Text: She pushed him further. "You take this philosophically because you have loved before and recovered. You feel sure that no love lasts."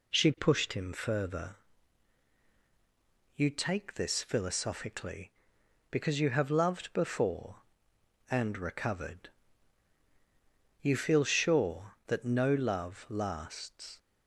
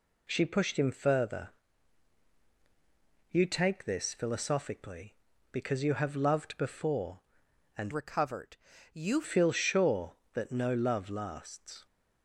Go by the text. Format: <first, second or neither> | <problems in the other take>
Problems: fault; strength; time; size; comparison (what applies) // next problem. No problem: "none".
first | changes voice from "recovered" to "You"; from 7.9 to 9.2 s; 1.3 s long